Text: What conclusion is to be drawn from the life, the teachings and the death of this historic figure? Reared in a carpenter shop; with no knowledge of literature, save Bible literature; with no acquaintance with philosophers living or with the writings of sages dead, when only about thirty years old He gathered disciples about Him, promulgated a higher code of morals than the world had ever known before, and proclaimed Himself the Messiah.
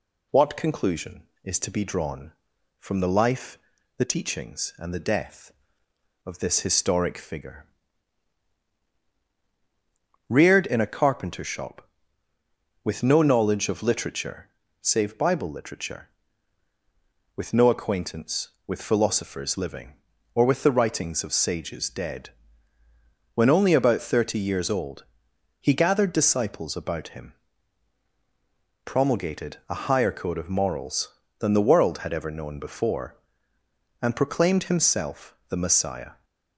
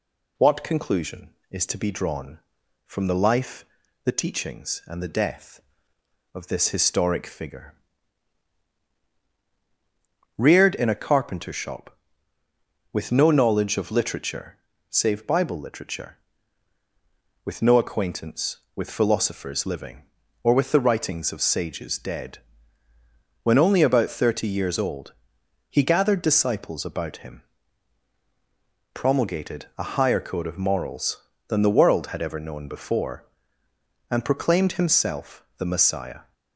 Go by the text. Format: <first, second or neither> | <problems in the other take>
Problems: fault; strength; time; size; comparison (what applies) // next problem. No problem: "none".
neither | pauses between "old" and "He"; noticeable; the same in both